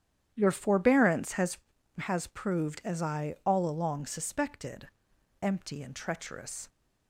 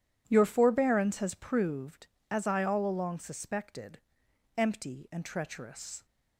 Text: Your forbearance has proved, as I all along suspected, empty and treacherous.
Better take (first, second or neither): second